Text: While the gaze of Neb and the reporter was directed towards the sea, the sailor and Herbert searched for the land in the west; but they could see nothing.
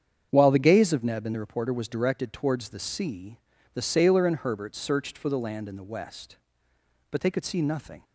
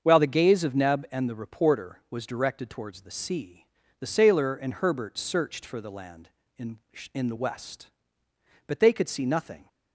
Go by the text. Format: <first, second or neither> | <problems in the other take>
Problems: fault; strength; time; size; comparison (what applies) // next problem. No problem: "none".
first | starts louder than the rest; until 1.0 s; 7 dB; strong in the first // says "in" twice; at 7.1 s